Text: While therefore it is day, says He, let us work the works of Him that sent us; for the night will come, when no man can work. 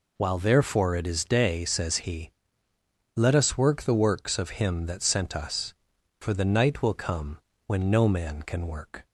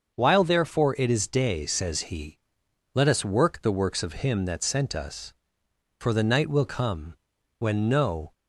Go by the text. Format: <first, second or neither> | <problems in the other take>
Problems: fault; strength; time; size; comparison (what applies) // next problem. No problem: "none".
first | starts louder than the rest; until 1.2 s; 6.5 dB // stops before "man can work"; at 8.3 s